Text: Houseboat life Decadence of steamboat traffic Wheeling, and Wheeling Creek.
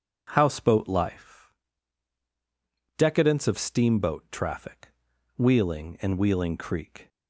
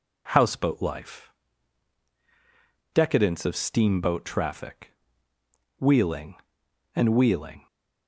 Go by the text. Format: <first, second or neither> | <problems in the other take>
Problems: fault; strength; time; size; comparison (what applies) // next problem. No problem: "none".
first | pauses between "life" and "Decadence"; strong; at 1.3 s; 1.6 s long; strong in the first // pauses between "traffic" and "Wheeling"; noticeable; at 4.9 s; 0.88 s long; noticeable in the first // stops before "Creek"; at 7.6 s